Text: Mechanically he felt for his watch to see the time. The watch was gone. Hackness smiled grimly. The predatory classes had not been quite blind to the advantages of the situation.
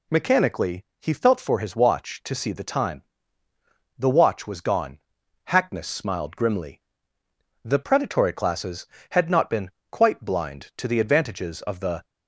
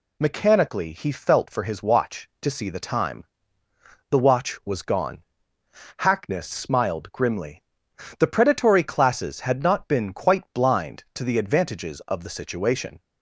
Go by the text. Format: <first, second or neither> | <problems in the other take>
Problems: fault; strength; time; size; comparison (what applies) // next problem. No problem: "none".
second | pauses between "been" and "quite"; slight; at 9.7 s; 0.20 s long // stops before "situation"; at 12.0 s